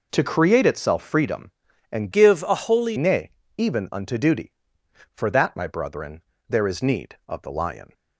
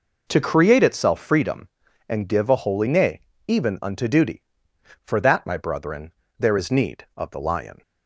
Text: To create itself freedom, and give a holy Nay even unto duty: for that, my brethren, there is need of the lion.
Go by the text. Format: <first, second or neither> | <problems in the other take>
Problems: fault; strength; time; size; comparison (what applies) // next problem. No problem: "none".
second | changes voice from "give" to "holy"; from 2.1 to 2.9 s; 0.8 s long // pauses between "Nay" and "even"; slight; at 3.3 s; 0.26 s long; slight in the second